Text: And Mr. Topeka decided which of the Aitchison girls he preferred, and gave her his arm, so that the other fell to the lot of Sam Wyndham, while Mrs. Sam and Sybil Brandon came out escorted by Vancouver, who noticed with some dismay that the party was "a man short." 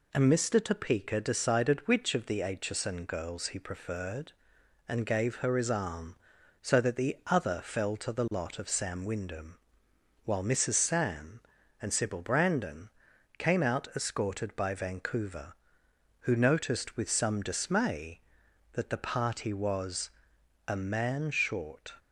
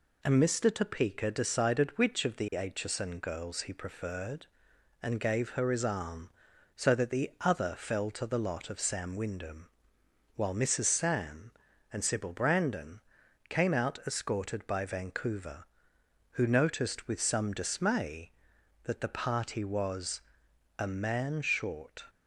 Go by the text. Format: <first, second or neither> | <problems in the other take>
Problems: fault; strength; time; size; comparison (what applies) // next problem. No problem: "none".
neither | pauses between "Brandon" and "came"; noticeable; the same in both // pauses between "was" and "a"; noticeable; the same in both